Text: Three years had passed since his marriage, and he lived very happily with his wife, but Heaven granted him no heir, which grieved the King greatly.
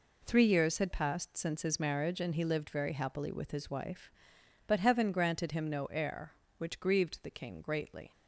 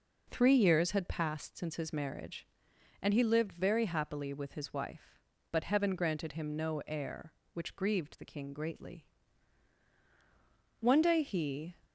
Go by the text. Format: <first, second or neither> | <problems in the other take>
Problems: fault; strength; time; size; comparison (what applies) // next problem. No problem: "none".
first | goes on to say "One day he"; noticeable; from 10.7 s on; 0.96 s long